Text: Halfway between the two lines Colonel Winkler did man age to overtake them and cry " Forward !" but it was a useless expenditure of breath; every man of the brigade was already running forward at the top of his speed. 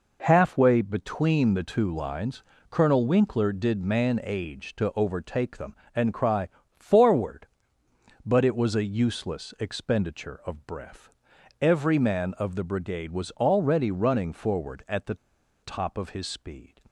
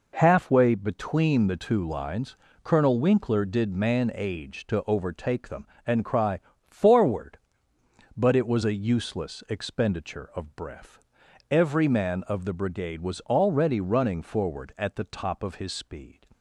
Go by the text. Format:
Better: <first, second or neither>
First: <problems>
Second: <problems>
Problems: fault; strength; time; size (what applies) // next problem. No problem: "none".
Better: second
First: pauses between "lines" and "Colonel"; slight; at 2.4 s; 0.26 s long // pauses between "the" and "top"; noticeable; at 15.1 s; 0.46 s long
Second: pauses between "lines" and "Colonel"; slight; at 2.3 s; 0.26 s long